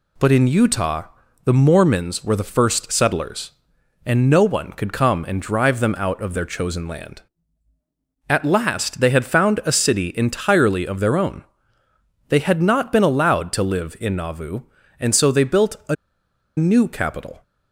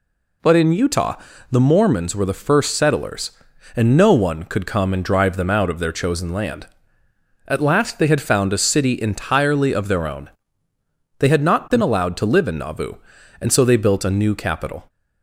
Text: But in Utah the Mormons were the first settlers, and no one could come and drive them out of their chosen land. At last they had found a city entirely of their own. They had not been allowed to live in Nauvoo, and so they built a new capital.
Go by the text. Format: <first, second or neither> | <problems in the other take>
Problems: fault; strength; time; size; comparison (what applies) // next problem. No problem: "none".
second | pauses between "Utah" and "the"; at 1.0 s; 0.40 s long; slight in the second // pauses between "a" and "new"; noticeable; at 15.9 s; 0.62 s long